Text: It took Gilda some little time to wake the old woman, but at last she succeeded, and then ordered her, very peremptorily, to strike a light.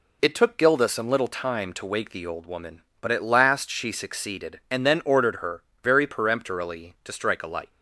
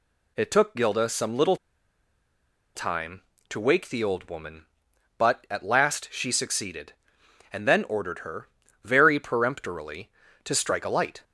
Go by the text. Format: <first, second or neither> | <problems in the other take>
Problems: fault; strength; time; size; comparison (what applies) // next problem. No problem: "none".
first | pauses between "little" and "time"; at 1.5 s; 1.1 s long